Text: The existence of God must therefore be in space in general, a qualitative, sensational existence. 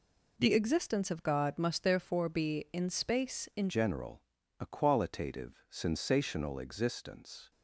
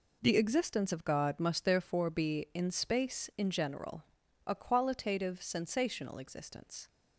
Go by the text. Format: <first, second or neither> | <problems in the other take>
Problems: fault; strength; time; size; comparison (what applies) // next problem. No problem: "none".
second | changes voice at "general"; from 3.6 s on; 3.9 s long